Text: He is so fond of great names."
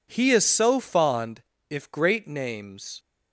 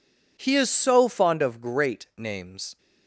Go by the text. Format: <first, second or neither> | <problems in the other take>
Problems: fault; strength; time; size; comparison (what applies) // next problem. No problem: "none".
second | says "if" for "of"; at 1.6 s